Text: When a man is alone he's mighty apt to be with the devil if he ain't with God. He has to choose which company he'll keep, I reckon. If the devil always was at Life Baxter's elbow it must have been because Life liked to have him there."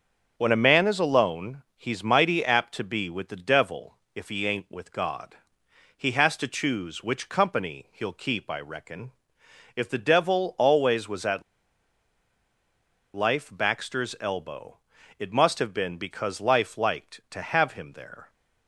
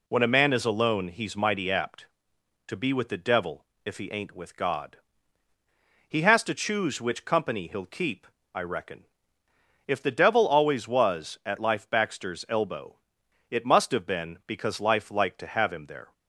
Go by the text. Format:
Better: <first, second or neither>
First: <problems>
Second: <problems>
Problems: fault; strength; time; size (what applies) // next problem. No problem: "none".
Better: second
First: starts louder than the rest; until 1.3 s; 7 dB // pauses between "alone" and "he's"; slight; at 1.6 s; 0.16 s long // pauses between "devil" and "if"; slight; at 3.9 s; 0.18 s long // pauses between "at" and "Life"; strong; at 11.4 s; 1.7 s long // pauses between "elbow" and "it"; at 14.7 s; 0.42 s long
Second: pauses between "devil" and "if"; slight; at 3.6 s; 0.20 s long // pauses between "elbow" and "it"; noticeable; at 12.9 s; 0.52 s long